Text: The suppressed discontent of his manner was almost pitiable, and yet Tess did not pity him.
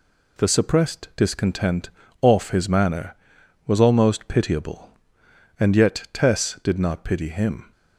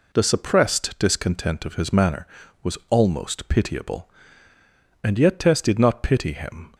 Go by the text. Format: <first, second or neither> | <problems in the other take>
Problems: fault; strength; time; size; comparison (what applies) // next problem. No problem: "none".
second | says "off" for "of"; at 2.2 s